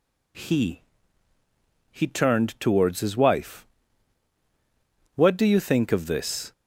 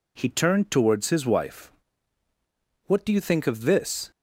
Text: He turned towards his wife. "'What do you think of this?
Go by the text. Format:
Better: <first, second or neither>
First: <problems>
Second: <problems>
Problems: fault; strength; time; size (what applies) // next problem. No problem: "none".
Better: second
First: says "He" twice; at 1.8 s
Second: none